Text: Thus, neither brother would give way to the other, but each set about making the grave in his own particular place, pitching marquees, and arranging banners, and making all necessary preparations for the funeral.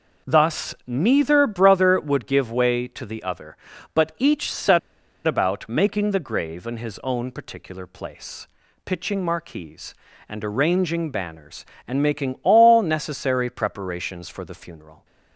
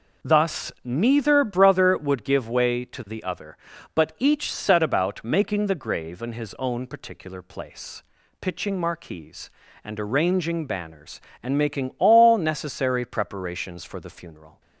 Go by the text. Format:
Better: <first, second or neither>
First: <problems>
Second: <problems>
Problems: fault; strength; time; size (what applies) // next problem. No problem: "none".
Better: second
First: pauses between "set" and "about"; noticeable; at 4.7 s; 0.47 s long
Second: none